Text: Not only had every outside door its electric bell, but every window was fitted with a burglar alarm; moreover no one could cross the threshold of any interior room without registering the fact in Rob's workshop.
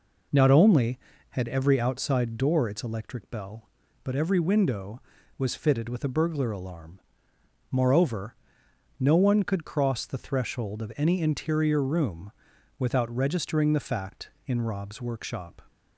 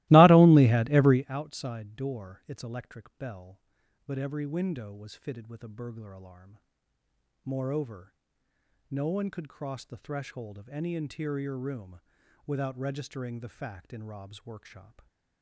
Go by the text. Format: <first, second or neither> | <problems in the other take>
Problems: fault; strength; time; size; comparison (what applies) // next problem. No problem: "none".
first | starts louder than the rest; strong; until 1.3 s; 19.5 dB // pauses between "moreover" and "no"; noticeable; at 8.1 s; 0.74 s long; noticeable in the first // pauses between "room" and "without"; noticeable; at 11.9 s; 0.46 s long; noticeable in the first